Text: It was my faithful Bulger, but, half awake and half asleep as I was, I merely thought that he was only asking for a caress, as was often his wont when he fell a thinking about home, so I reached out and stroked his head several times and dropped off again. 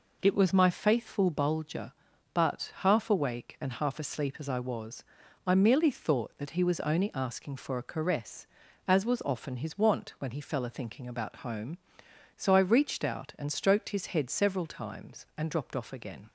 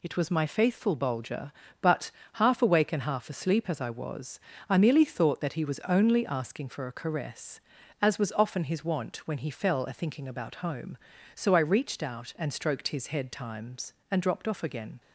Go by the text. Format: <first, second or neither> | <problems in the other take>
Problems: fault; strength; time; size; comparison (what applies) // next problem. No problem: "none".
first | skips "several"; at 13.3 s